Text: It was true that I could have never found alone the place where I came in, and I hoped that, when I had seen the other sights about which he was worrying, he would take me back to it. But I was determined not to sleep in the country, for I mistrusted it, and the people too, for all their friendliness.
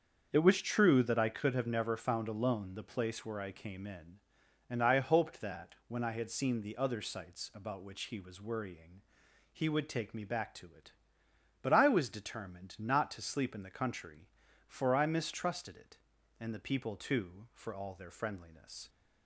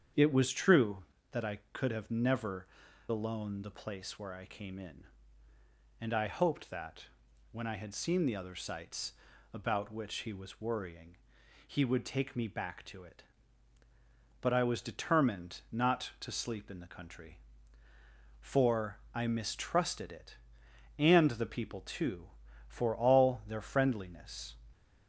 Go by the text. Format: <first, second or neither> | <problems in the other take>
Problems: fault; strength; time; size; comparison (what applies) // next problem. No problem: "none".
first | starts louder than the rest; strong; until 1.4 s; 8 dB; also in the first // skips "found"; at 2.8 s // pauses between "sights" and "about"; at 9.1 s; 0.38 s long